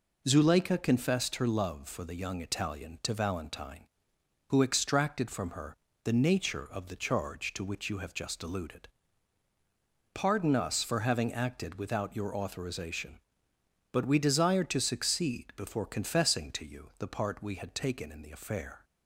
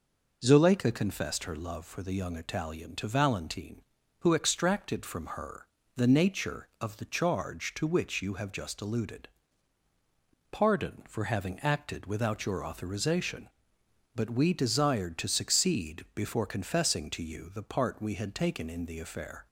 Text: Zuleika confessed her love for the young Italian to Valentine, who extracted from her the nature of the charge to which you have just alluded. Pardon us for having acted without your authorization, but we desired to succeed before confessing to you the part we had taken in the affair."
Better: first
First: pauses between "her" and "the"; slight; at 5.7 s; 0.26 s long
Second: pauses between "her" and "the"; slight; at 5.6 s; 0.28 s long // skips "us"; at 11.0 s

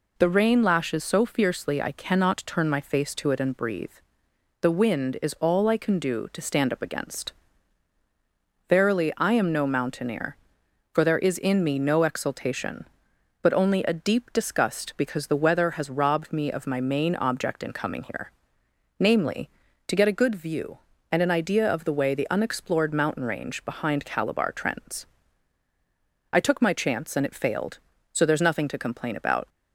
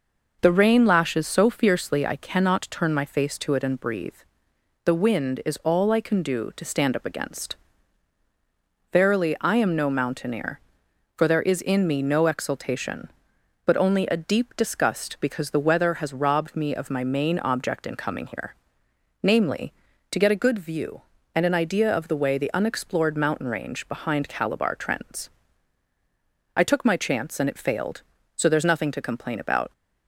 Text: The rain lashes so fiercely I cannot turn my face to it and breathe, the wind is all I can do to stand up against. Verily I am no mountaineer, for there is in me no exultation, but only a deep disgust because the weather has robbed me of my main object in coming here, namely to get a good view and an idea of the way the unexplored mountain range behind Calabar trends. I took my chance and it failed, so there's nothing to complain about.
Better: first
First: none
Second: starts louder than the rest; noticeable; until 2.2 s; 5.5 dB

